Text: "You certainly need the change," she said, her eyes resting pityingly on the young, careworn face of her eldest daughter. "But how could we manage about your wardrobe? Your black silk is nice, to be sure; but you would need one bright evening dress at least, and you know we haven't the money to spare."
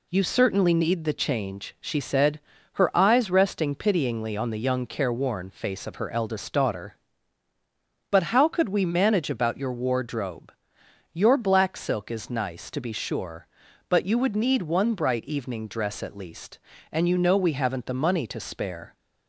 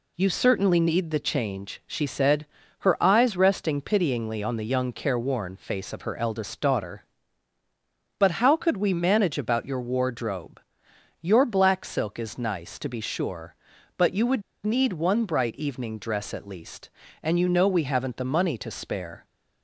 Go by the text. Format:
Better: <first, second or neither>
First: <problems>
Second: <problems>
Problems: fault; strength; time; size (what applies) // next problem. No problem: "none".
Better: first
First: none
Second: pauses between "would" and "need"; slight; at 14.4 s; 0.23 s long